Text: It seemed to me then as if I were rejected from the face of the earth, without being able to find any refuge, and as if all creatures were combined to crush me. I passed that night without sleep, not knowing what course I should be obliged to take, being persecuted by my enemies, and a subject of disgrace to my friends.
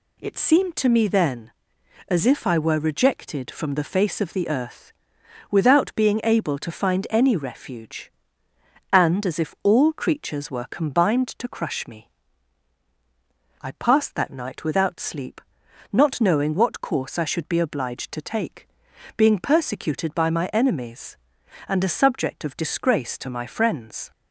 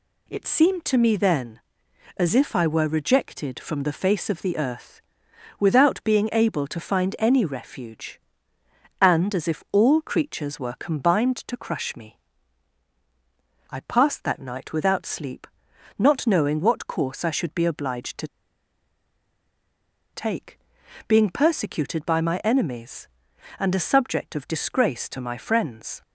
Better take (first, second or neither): first